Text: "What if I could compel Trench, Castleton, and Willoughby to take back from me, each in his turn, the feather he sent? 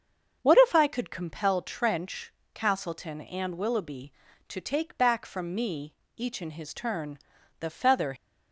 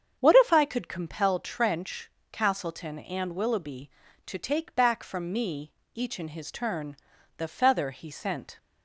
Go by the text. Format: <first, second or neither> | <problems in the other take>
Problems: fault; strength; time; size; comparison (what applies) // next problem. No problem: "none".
second | starts louder than the rest; noticeable; until 1.4 s; 6 dB; also in the second // stops before "he sent"; at 8.1 s